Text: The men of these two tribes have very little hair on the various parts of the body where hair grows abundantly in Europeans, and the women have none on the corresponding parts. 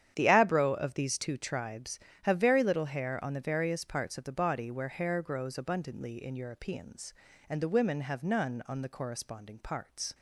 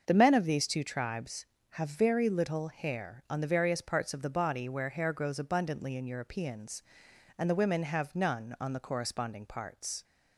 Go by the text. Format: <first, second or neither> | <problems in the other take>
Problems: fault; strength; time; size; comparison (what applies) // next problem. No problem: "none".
second | starts louder than the rest; strong; until 1.1 s; 9.5 dB; also in the second // says "abro" for "men"; at 0.2 s